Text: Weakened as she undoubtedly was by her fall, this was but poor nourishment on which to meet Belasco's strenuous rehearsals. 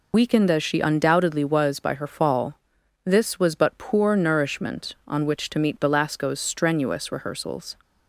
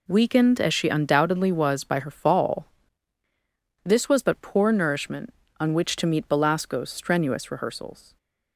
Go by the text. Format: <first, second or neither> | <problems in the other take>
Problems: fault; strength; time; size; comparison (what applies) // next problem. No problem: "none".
second | loses the start of "Weakened"; at 0.1 s; 75 ms